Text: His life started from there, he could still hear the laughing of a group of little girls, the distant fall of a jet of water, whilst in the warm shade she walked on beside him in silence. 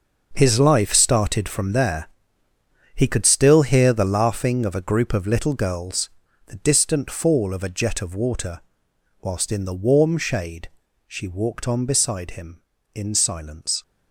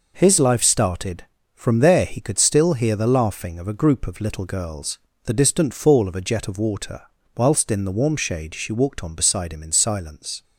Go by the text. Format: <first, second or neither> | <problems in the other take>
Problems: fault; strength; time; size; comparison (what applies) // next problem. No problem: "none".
second | gets quieter; strong; throughout; 11.5 dB // pauses between "shade" and "she"; at 10.6 s; 0.40 s long